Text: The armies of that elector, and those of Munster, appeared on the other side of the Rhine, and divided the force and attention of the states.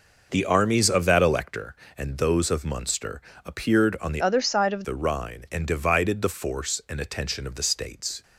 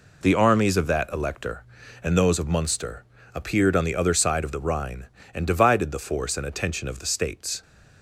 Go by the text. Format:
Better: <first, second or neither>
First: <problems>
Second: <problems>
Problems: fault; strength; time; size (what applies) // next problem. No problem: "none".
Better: second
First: changes voice from "other" to "of"; from 4.2 to 4.8 s; 0.6 s long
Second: none